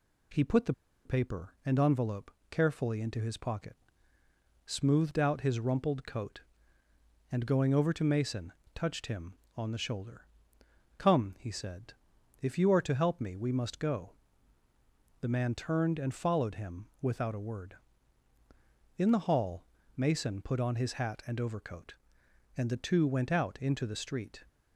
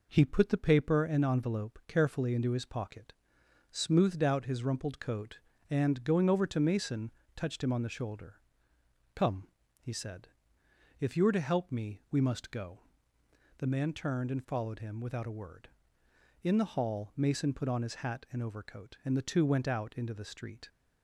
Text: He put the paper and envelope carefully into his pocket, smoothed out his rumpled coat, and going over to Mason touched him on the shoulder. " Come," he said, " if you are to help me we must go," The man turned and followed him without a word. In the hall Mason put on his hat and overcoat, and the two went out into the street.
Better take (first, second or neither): second